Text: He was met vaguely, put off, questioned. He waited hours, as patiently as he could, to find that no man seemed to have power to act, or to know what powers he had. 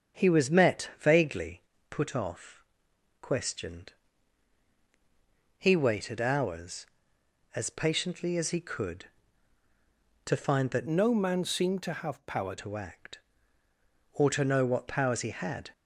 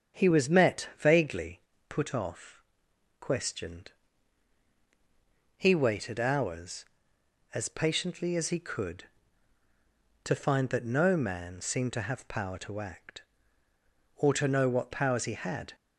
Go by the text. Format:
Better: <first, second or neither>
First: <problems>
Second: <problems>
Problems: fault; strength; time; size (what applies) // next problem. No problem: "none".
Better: second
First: starts louder than the rest; strong; until 1.2 s; 7.5 dB // changes voice from "no" to "power"; from 10.8 to 12.5 s; 1.7 s long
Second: starts louder than the rest; strong; until 1.2 s; 8 dB